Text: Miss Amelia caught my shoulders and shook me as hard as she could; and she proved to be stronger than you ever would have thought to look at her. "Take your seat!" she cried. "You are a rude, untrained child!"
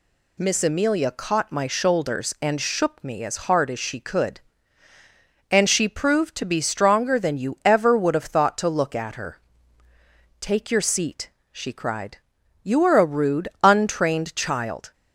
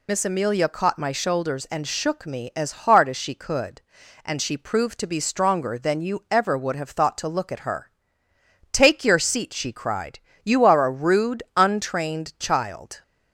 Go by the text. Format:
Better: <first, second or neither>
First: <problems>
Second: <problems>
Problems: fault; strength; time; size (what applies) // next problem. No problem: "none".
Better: first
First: none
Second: loses the start of "Miss"; at 0.0 s; 45 ms